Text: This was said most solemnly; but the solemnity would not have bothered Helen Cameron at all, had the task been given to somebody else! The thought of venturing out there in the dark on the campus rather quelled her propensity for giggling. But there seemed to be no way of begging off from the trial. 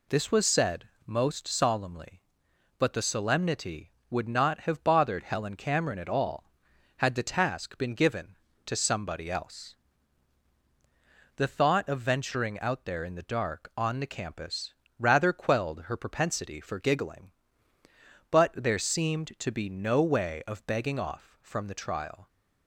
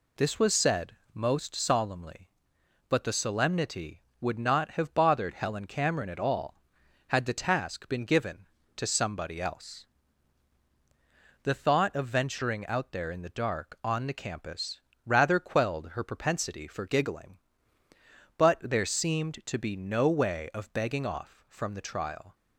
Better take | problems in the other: neither | pauses between "said" and "most"; slight; the same in both // pauses between "campus" and "rather"; slight; the same in both

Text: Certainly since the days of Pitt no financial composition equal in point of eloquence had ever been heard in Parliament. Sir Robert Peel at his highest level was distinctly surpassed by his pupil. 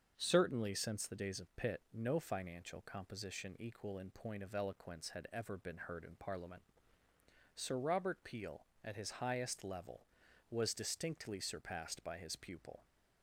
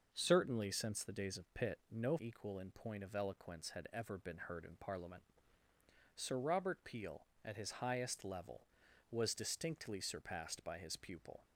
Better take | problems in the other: first | starts louder than the rest; noticeable; until 1.1 s; 6 dB; also in the first // skips "financial composition"; at 2.1 s

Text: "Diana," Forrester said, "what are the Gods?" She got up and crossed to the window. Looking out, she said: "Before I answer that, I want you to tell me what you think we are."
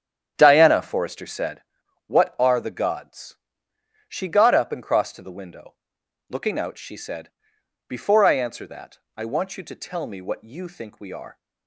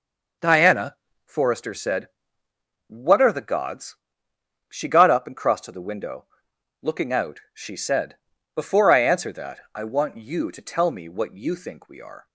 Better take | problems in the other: second | starts louder than the rest; strong; until 1.7 s; 9 dB

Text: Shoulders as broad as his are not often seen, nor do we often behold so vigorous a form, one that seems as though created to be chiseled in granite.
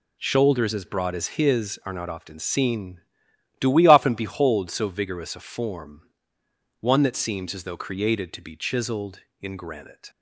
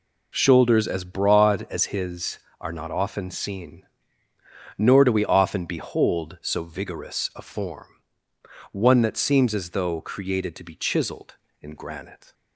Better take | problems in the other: second | skips "nor"; at 3.3 s

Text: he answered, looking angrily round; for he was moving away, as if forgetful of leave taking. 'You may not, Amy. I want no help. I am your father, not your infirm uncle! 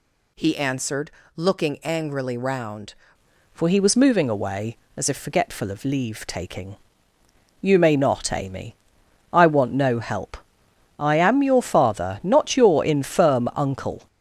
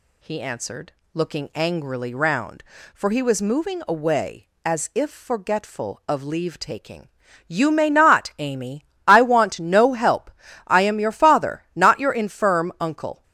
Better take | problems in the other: second | changes voice at "for"; from 3.5 s on; 10.5 s long

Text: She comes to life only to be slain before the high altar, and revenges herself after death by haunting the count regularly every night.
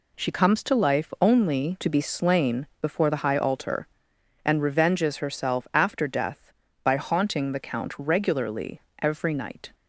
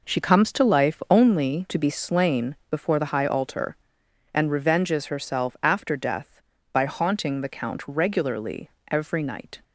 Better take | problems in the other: first | starts louder than the rest; noticeable; until 1.6 s; 5 dB // pauses between "regularly" and "every"; slight; at 8.6 s; 0.22 s long; slight in the first

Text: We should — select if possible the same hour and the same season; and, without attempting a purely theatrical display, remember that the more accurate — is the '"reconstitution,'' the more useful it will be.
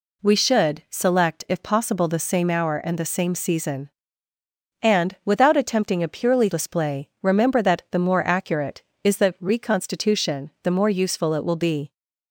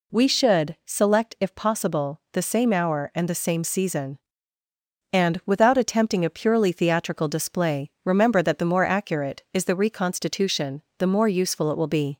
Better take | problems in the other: second | skips "theatrical"; at 6.5 s

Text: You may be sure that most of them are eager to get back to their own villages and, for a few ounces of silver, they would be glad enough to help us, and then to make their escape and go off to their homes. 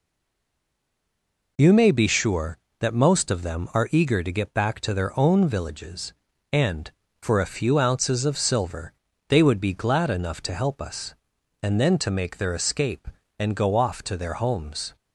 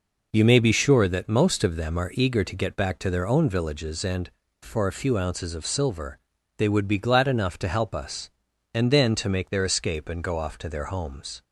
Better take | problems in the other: second | stays silent before the first word; noticeable; until 1.5 s; 1.5 s long

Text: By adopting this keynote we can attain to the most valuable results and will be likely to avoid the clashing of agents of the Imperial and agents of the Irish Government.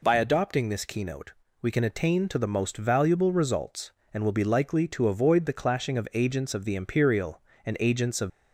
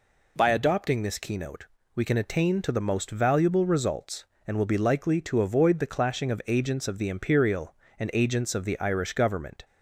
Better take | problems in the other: second | pauses between "keynote" and "we"; slight; at 1.3 s; 0.30 s long; slight in the second // stops before "the Irish Government"; at 8.2 s

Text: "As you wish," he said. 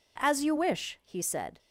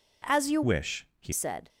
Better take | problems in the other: first | changes voice from "wish" to "he"; from 0.6 to 1.3 s; 0.7 s long

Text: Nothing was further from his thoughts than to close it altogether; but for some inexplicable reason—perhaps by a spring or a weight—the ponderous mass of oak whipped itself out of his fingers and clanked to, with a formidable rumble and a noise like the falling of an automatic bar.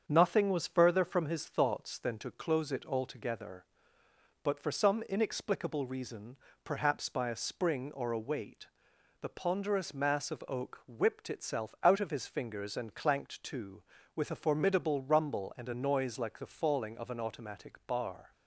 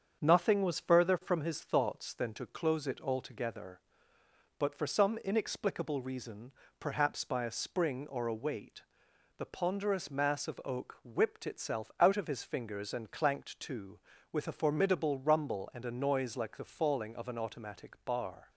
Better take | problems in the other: neither | starts louder than the rest; strong; the same in both

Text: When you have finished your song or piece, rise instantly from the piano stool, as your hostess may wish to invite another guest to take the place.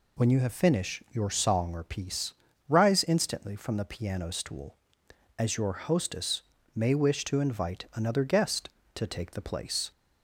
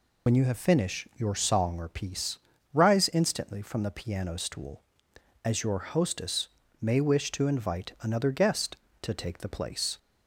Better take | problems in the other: first | loses the start of "When"; at 0.2 s; 45 ms // pauses between "hostess" and "may"; slight; at 6.4 s; 0.32 s long; slight in the first

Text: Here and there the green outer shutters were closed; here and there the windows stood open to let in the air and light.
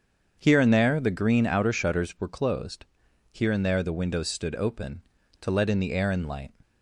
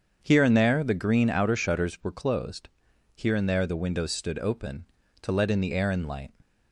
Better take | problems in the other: neither | starts louder than the rest; the same in both

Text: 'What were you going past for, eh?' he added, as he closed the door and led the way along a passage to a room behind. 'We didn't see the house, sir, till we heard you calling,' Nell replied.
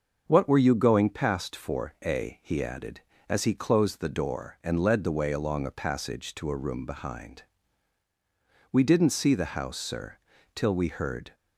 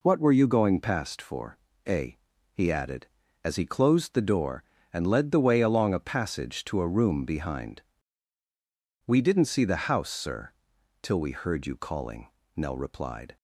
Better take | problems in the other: second | starts louder than the rest; until 1.2 s; 6.5 dB // stops before "you calling Nell replied"; at 11.3 s

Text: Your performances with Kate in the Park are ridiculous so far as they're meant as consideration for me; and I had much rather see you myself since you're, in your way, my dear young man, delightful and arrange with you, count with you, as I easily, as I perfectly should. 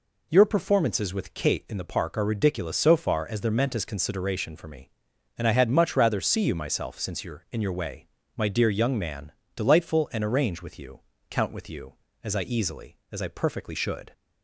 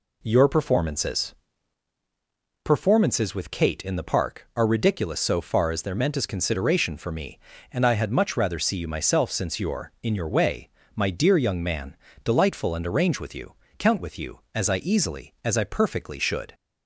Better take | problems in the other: first | says "performances" twice; at 2.6 s

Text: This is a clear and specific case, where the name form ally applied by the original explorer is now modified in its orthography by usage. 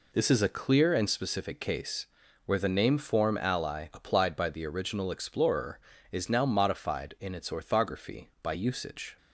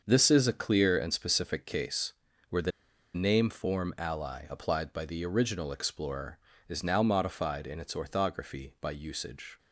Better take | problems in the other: first | starts louder than the rest; until 1.0 s; 6.5 dB // pauses between "the" and "name"; at 2.7 s; 0.44 s long

